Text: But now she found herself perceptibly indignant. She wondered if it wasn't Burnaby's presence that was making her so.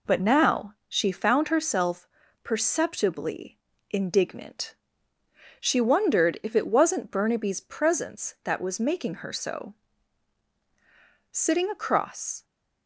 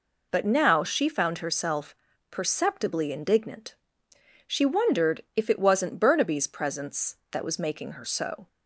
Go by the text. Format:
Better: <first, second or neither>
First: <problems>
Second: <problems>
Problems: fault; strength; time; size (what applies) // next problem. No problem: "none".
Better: second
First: pauses between "herself" and "perceptibly"; at 2.0 s; 0.38 s long // pauses between "perceptibly" and "indignant"; slight; at 3.5 s; 0.32 s long // goes on to say "Sitting across"; noticeable; from 11.3 s on; 1.1 s long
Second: pauses between "herself" and "perceptibly"; slight; at 1.9 s; 0.36 s long